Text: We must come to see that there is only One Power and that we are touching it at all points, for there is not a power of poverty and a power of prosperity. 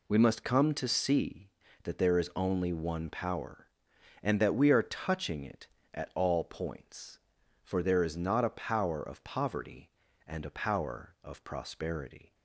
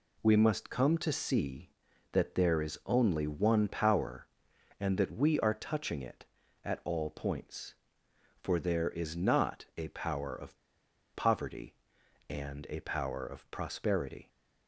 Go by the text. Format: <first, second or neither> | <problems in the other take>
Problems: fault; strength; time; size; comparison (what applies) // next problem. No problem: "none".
first | pauses between "of" and "poverty"; noticeable; at 10.5 s; 0.59 s long